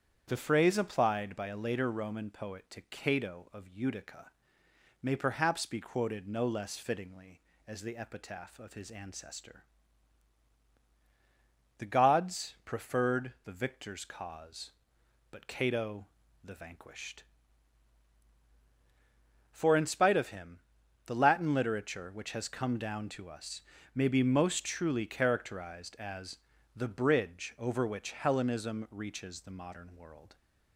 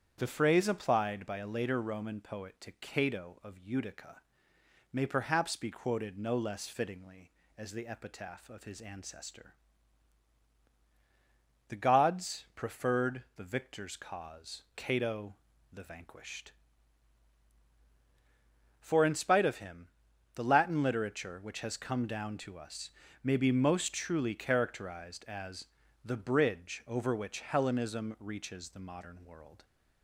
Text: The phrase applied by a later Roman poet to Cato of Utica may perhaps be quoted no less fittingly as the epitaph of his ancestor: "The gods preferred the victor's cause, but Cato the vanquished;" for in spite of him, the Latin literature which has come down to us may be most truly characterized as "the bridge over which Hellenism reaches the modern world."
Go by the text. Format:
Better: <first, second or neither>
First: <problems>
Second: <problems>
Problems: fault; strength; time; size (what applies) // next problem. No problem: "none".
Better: first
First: starts louder than the rest; strong; until 1.2 s; 8.5 dB // pauses between "Utica" and "may"; noticeable; at 4.2 s; 0.74 s long // pauses between "Cato" and "the"; slight; at 16.0 s; 0.36 s long // pauses between "us" and "may"; slight; at 23.6 s; 0.34 s long // pauses between "as" and "the"; slight; at 26.3 s; 0.36 s long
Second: starts louder than the rest; strong; until 1.1 s; 8.5 dB // pauses between "Utica" and "may"; noticeable; at 4.1 s; 0.74 s long // skips "but"; at 14.6 s // pauses between "Cato" and "the"; slight; at 15.3 s; 0.36 s long // pauses between "us" and "may"; slight; at 22.8 s; 0.34 s long // pauses between "as" and "the"; slight; at 25.6 s; 0.36 s long